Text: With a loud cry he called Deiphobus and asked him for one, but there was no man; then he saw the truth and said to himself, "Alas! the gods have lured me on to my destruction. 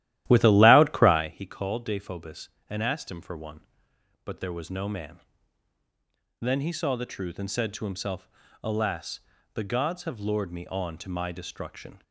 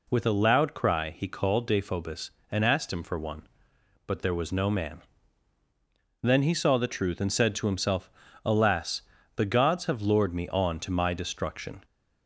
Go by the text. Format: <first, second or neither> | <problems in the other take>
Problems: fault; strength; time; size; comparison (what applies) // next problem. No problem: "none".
second | starts louder than the rest; strong; until 1.4 s; 13.5 dB